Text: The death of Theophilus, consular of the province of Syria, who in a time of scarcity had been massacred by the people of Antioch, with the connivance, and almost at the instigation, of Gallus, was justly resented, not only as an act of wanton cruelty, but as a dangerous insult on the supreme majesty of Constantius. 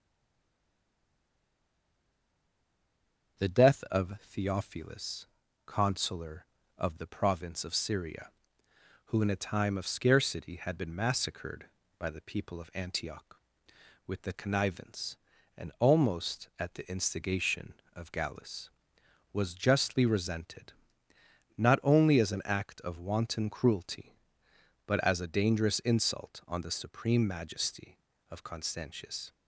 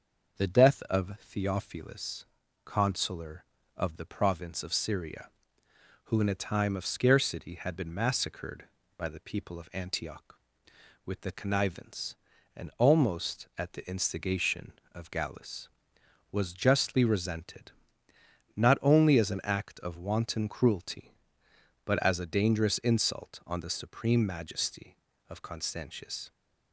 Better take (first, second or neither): second